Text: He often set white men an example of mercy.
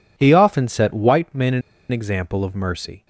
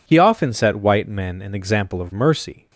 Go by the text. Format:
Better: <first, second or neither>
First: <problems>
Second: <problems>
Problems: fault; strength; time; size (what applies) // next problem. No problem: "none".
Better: second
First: pauses between "an" and "example"; slight; at 1.6 s; 0.30 s long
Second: none